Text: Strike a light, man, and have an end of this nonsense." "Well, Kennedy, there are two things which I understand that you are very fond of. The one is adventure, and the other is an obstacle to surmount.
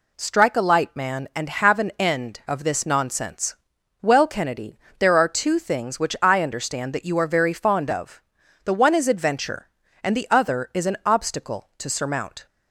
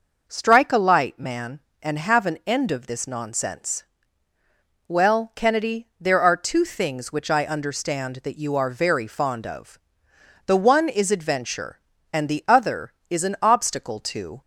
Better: first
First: none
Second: stops before "surmount"; at 14.4 s

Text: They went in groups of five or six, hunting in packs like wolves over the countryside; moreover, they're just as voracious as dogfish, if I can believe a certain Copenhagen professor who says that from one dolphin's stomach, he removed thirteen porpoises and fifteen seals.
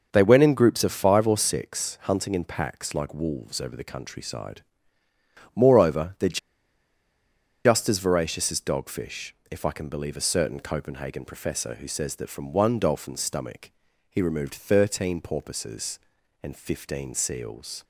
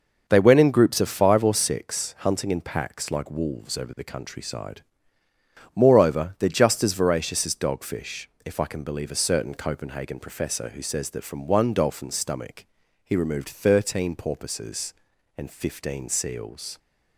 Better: second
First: starts louder than the rest; noticeable; until 1.1 s; 6 dB // pauses between "they're" and "just"; strong; at 6.3 s; 1.2 s long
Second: starts louder than the rest; noticeable; until 1.3 s; 6 dB

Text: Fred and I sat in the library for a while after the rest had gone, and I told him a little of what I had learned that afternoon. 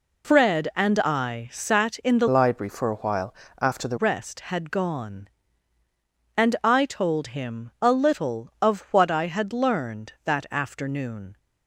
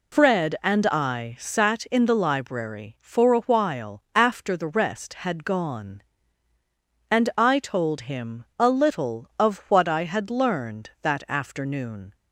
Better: second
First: changes voice from "library" to "the"; from 2.2 to 3.9 s; 1.7 s long // pauses between "while" and "after"; slight; at 3.3 s; 0.26 s long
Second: none

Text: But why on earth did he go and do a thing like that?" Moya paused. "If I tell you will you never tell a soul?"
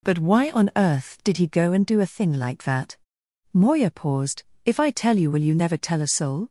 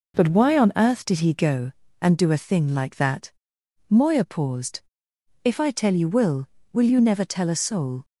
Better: first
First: none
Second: says "will" twice; at 6.7 s

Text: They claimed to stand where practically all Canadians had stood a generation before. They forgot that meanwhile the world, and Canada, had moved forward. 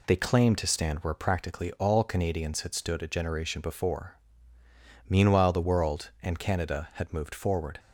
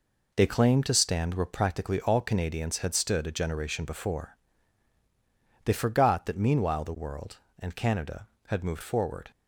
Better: second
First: skips "They forgot that"; at 4.6 s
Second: none

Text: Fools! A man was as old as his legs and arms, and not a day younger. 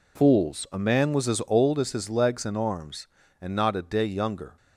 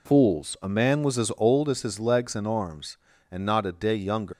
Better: first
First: none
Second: leaves "younger" unfinished; at 4.3 s; 130 ms

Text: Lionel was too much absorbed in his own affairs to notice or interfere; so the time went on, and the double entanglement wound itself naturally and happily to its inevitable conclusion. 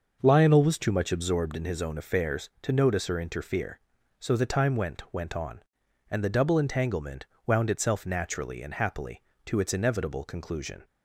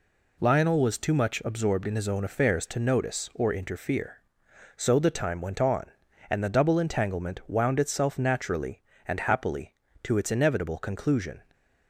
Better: second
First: starts louder than the rest; noticeable; until 1.2 s; 6 dB // says "went" twice; at 5.1 s // pauses between "entanglement" and "wound"; slight; at 7.2 s; 0.18 s long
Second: none

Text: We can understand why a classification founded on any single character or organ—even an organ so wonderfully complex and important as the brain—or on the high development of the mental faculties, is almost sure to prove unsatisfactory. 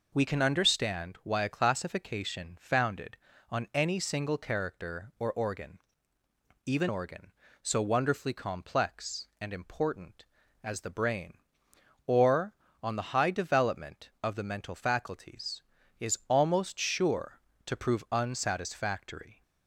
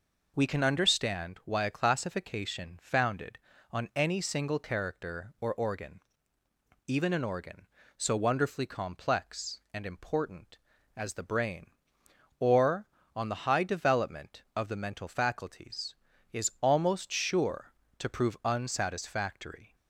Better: second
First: skips "an"; at 6.8 s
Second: none

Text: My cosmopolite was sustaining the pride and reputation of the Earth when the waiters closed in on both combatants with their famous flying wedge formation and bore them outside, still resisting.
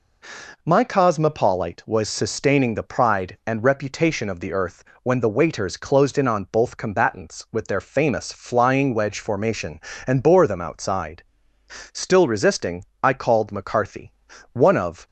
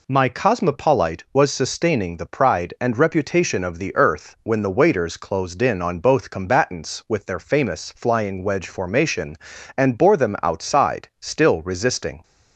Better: second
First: pauses between "Earth" and "when"; slight; at 4.8 s; 0.20 s long // goes on to say "I called McCarthy one of"; strong; from 13.0 s on; 2.0 s long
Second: none

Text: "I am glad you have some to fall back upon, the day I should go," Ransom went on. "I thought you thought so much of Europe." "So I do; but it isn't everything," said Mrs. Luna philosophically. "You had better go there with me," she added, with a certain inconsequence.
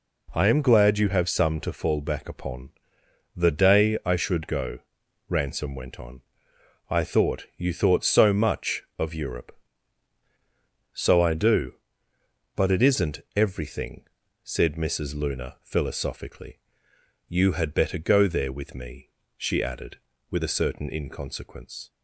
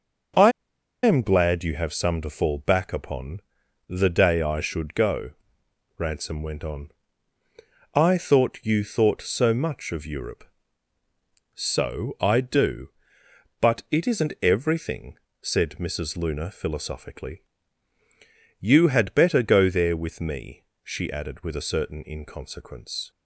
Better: first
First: none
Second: starts louder than the rest; until 1.9 s; 6 dB // pauses between "I" and "am"; noticeable; at 0.5 s; 0.52 s long

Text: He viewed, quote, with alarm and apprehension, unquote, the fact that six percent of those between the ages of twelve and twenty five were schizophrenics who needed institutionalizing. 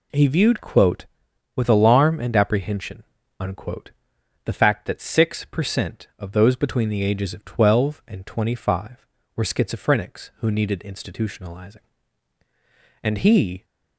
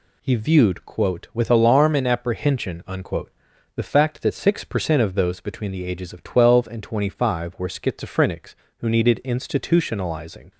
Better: second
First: goes on to say "And he"; noticeable; from 13.0 s on; 0.62 s long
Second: none

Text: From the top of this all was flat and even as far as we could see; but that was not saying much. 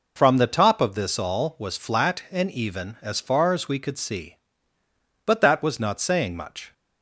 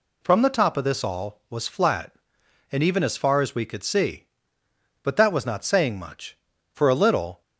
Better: first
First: none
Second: goes on to say "For a little"; noticeable; from 6.7 s on; 0.66 s long

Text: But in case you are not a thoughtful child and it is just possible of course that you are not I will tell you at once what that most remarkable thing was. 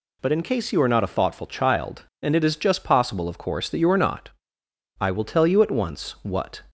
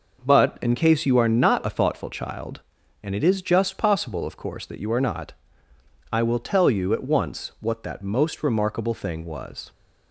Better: second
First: pauses between "not" and "I"; noticeable; at 4.2 s; 0.70 s long // stops before "that most remarkable thing was"; at 6.6 s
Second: pauses between "not" and "I"; noticeable; at 5.3 s; 0.78 s long

